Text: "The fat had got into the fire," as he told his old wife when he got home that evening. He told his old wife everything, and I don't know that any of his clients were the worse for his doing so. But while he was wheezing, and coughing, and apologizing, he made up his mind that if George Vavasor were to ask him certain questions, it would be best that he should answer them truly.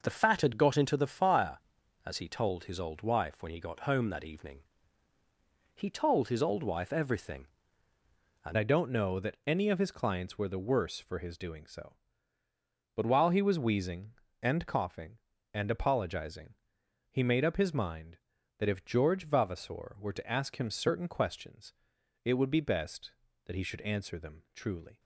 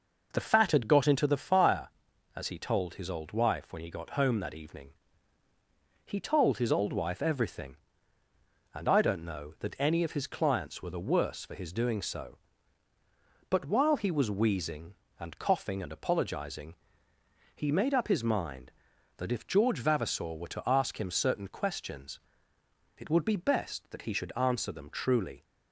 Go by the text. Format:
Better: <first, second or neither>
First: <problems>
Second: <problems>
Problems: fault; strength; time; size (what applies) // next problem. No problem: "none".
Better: second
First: changes voice at "I"; from 8.5 s on; 16.4 s long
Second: none